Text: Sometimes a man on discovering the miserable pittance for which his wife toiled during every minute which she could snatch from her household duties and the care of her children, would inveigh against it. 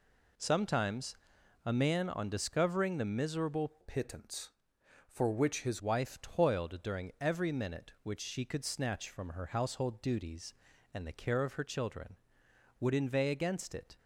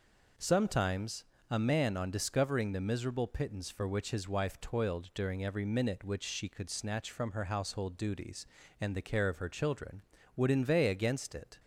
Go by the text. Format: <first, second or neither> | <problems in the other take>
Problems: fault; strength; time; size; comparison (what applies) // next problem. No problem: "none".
second | pauses between "Sometimes" and "a"; noticeable; at 1.1 s; 0.50 s long; slight in the second // changes voice from "pittance" to "his"; from 3.8 to 5.8 s; 2.0 s long